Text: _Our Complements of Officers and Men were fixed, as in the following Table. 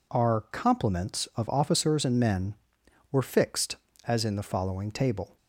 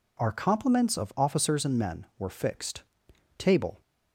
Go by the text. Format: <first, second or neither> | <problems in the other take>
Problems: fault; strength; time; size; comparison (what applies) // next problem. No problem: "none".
first | skips "as in the following"; at 3.1 s